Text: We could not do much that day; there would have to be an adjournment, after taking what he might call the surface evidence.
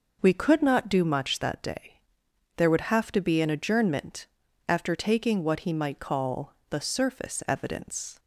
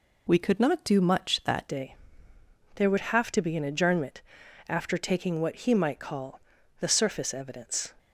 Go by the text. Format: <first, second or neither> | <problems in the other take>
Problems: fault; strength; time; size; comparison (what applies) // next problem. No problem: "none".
first | changes voice at "day"; from 1.6 s on; 6.3 s long // pauses between "call" and "the"; at 6.3 s; 0.40 s long; slight in the first